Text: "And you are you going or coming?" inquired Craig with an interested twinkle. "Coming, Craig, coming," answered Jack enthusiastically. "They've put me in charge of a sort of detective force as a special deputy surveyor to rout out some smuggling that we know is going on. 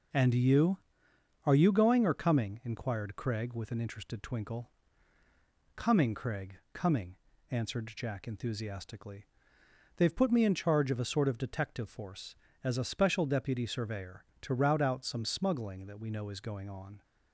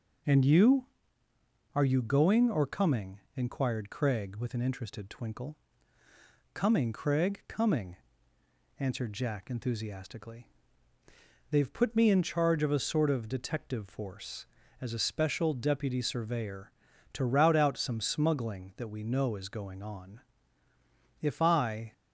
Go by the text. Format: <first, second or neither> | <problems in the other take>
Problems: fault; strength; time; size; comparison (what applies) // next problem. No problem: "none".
first | goes on to say "If I"; noticeable; from 21.2 s on; 0.70 s long